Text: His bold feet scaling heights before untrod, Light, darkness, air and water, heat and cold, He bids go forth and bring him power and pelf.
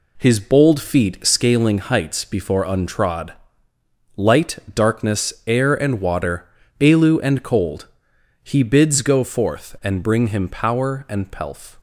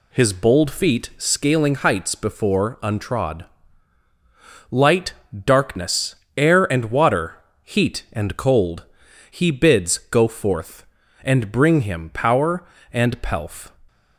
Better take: second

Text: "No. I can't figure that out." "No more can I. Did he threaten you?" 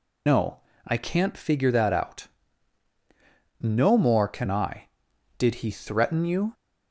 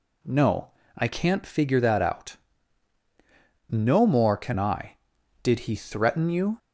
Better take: second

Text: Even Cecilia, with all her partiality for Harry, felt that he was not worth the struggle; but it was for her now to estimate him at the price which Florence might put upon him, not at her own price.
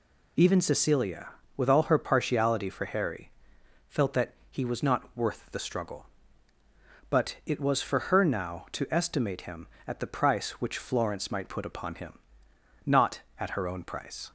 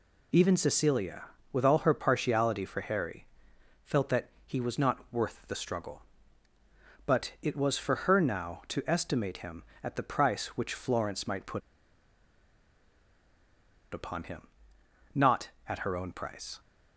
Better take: first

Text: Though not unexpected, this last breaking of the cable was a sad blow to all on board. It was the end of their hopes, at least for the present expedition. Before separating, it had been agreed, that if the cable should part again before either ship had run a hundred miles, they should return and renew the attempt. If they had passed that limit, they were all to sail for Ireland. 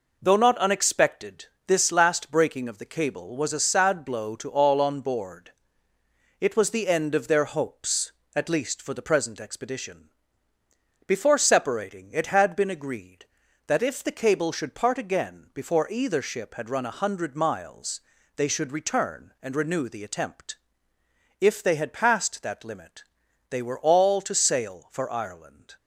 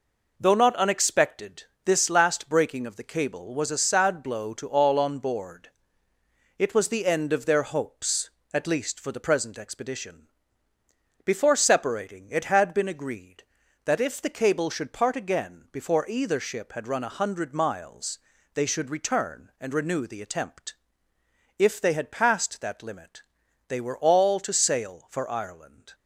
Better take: neither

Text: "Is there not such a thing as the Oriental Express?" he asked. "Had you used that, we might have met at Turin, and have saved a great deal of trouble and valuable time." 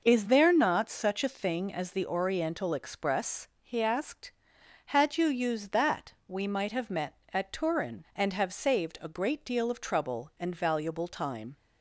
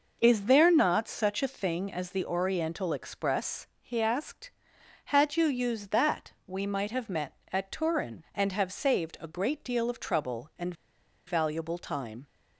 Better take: first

